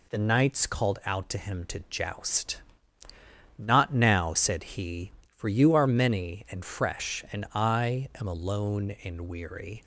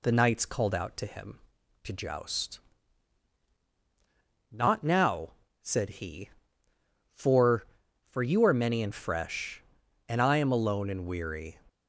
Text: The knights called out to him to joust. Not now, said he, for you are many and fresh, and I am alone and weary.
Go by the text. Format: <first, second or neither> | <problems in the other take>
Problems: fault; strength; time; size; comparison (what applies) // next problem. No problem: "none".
first | says "for" twice; at 8.0 s